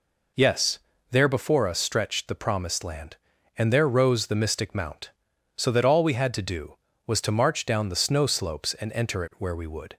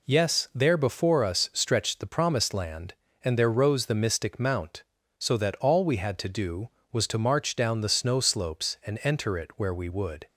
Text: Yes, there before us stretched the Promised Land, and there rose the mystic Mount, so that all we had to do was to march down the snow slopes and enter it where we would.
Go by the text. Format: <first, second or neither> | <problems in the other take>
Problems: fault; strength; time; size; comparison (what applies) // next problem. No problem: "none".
neither | none